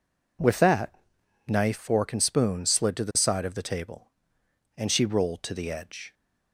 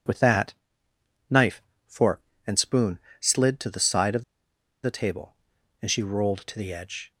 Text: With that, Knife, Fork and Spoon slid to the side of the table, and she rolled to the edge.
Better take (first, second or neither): first